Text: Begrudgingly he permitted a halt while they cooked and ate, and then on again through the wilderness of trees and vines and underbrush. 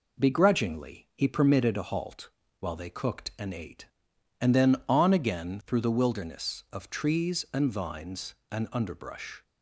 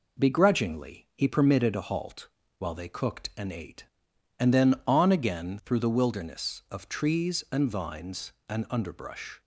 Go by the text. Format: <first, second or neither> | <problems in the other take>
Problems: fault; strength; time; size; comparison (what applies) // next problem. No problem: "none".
neither | pauses between "halt" and "while"; slight; the same in both